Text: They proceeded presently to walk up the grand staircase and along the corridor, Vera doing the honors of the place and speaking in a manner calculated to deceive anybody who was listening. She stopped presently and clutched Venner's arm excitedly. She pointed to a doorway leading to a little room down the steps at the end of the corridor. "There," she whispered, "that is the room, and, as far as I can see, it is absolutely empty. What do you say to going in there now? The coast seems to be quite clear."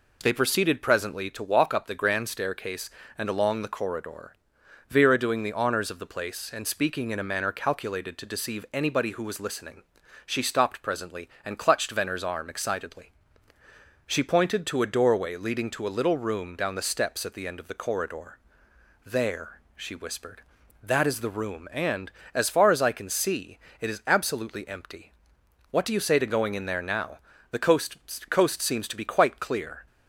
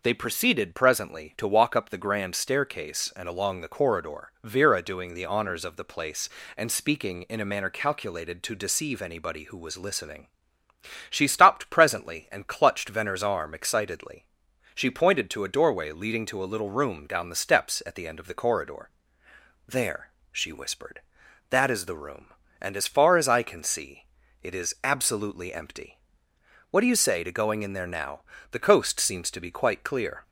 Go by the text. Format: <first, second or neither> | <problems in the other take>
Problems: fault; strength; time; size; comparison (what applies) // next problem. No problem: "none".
second | says "coast" twice; at 28.2 s